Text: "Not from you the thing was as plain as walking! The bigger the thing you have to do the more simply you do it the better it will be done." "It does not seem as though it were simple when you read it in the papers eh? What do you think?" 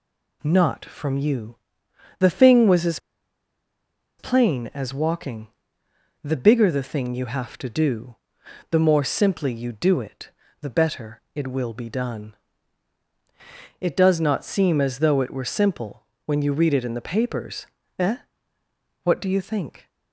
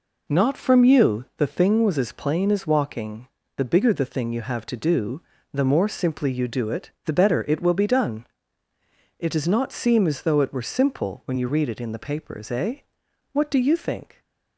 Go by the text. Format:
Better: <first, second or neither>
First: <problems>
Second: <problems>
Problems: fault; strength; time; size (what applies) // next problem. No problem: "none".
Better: second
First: pauses between "you" and "the"; noticeable; at 1.5 s; 0.62 s long // pauses between "as" and "plain"; at 2.9 s; 1.2 s long // pauses between "do" and "the"; noticeable; at 8.1 s; 0.56 s long // pauses between "it" and "the"; slight; at 10.3 s; 0.30 s long // pauses between "simple" and "when"; slight; at 16.0 s; 0.20 s long // pauses between "papers" and "eh"; slight; at 17.6 s; 0.32 s long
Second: pauses between "do" and "the"; slight; at 5.2 s; 0.32 s long // pauses between "it" and "the"; slight; at 6.8 s; 0.16 s long